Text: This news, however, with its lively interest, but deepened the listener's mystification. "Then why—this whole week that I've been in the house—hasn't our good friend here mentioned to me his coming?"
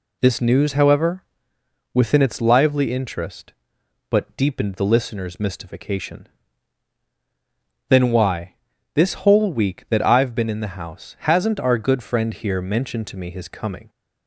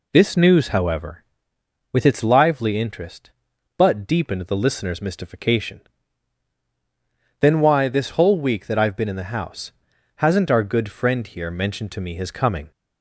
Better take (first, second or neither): second